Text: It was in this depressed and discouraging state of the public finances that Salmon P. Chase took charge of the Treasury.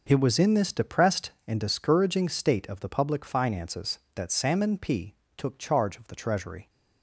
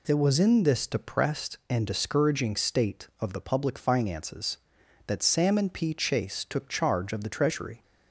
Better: second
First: skips "Chase"; at 5.2 s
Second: none

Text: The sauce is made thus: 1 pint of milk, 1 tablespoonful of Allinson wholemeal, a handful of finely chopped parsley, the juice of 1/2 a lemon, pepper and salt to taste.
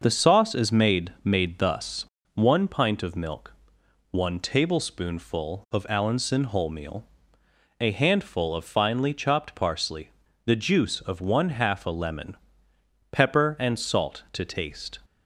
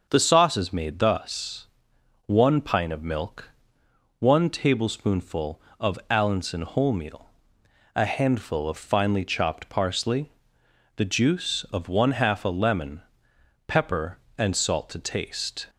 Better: second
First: starts louder than the rest; noticeable; until 1.0 s; 6 dB // says "made" twice; at 1.2 s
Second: starts louder than the rest; until 1.1 s; 6.5 dB

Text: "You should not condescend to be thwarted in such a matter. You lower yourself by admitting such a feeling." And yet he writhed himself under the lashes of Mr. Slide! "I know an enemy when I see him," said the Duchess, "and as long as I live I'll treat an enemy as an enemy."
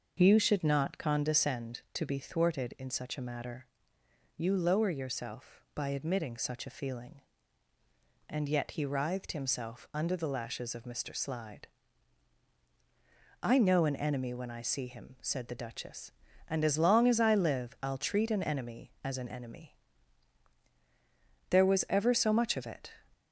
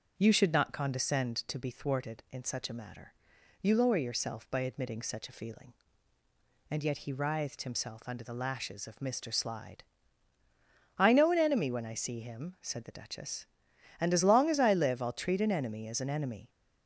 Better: second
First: starts louder than the rest; noticeable; until 1.2 s; 6 dB // goes on to say "There was ever so much of it"; from 21.4 s on; 1.4 s long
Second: starts louder than the rest; until 1.1 s; 6.5 dB

